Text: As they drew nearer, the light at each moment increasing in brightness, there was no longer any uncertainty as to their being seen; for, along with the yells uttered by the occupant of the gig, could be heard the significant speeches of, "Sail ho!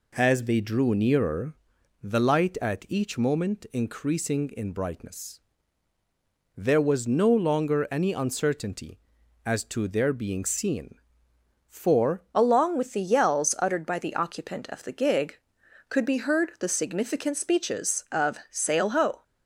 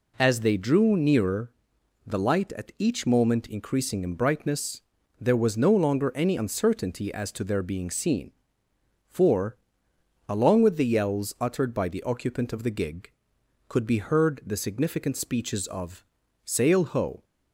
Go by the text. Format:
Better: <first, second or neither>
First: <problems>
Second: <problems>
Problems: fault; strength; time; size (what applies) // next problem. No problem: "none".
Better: second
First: changes voice at "along"; from 12.3 s on; 6.9 s long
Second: none